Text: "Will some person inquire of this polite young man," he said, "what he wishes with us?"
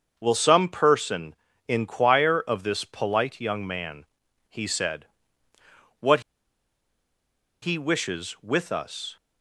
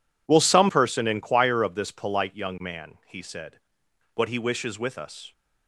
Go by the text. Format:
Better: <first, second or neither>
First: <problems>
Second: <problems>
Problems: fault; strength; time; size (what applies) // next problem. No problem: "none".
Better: second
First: starts louder than the rest; until 1.1 s; 6.5 dB // pauses between "person" and "inquire"; slight; at 1.3 s; 0.34 s long // pauses between "what" and "he"; strong; at 6.2 s; 1.4 s long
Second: none